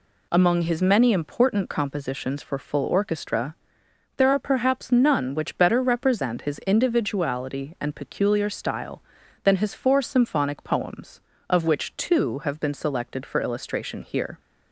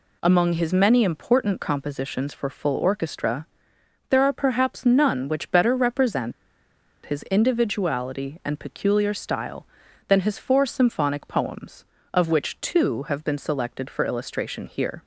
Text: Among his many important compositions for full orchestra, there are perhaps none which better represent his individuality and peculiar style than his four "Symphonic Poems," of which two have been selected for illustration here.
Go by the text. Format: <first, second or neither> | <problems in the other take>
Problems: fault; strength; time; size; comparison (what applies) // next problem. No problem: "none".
first | pauses between "represent" and "his"; noticeable; at 6.3 s; 0.73 s long